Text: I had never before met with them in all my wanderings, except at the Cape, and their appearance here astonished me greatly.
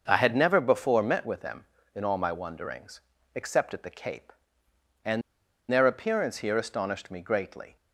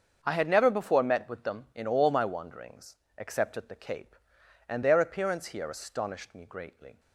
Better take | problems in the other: second | starts louder than the rest; until 1.0 s; 6 dB; also in the second // pauses between "and" and "their"; noticeable; at 5.2 s; 0.50 s long

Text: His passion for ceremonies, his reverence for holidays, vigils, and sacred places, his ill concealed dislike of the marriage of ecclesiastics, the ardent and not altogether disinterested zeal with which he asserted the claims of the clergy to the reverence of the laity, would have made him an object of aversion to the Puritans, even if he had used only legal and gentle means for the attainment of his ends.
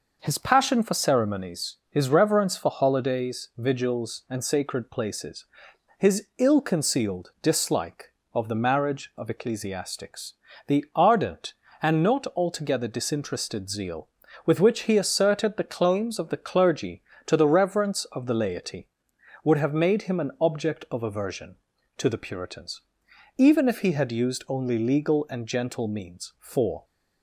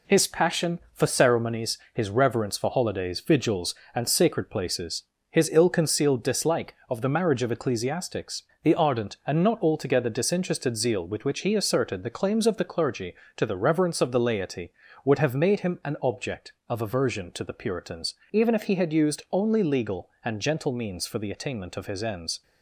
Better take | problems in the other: second | stops before "the attainment of his ends"; at 26.8 s

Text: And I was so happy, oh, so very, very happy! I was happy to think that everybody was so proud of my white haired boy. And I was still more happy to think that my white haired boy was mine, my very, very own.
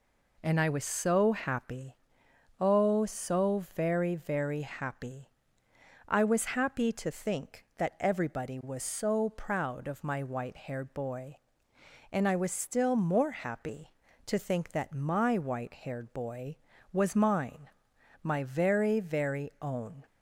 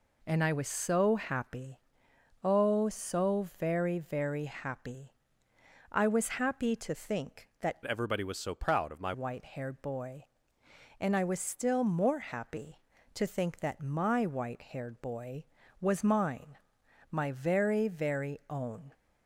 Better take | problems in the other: first | changes voice from "everybody" to "my"; from 7.8 to 9.1 s; 1.3 s long

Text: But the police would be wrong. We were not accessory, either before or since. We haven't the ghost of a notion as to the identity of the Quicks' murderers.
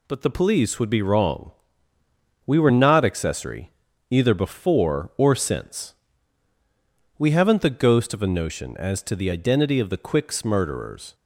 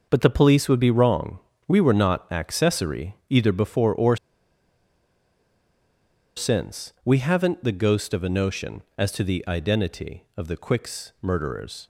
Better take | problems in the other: first | starts louder than the rest; noticeable; until 1.1 s; 6 dB // pauses between "or" and "since"; strong; at 4.1 s; 2.2 s long

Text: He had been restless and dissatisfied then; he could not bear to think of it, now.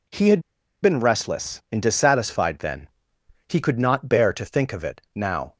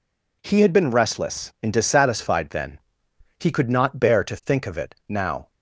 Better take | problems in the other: second | pauses between "had" and "been"; at 0.3 s; 0.43 s long

